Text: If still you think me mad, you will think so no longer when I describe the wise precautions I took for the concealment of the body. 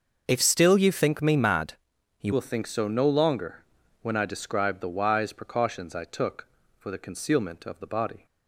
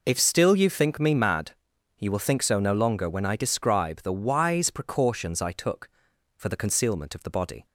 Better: second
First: starts louder than the rest; noticeable; until 1.2 s; 6 dB // changes voice at "will"; from 2.3 s on; 5.9 s long // pauses between "longer" and "when"; at 3.6 s; 0.38 s long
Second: none

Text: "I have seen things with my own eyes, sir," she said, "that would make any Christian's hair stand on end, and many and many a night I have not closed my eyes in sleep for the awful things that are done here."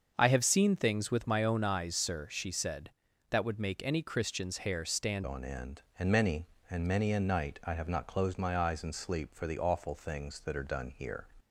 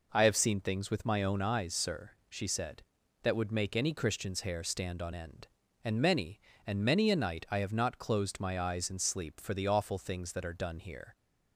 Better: second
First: starts louder than the rest; until 1.1 s; 6.5 dB // changes voice at "on"; from 5.2 s on; 6.0 s long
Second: none

